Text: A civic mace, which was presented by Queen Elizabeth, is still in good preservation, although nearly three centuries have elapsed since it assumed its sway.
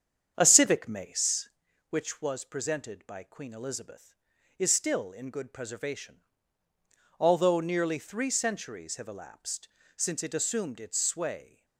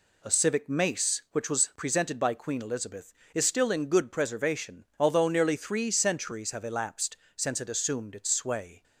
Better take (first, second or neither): second